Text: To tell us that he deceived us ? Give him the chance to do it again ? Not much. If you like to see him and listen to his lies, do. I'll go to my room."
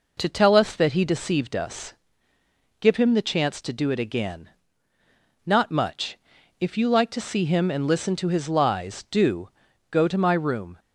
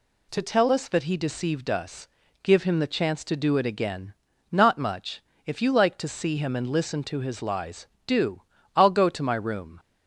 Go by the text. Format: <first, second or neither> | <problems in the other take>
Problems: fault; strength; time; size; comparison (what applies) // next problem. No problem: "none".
second | skips "I'll"; at 9.6 s